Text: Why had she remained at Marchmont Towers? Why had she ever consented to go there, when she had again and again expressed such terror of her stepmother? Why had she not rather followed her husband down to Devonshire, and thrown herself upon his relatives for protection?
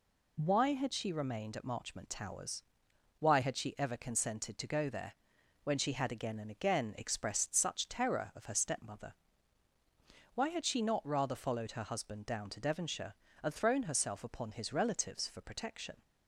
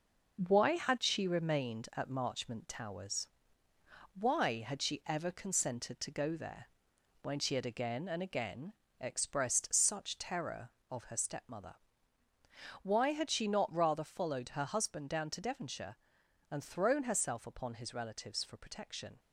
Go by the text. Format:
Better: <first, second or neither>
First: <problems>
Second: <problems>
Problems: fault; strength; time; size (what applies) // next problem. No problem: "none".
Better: first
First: none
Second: gets quieter; throughout; 6.5 dB // pauses between "again" and "expressed"; slight; at 8.7 s; 0.26 s long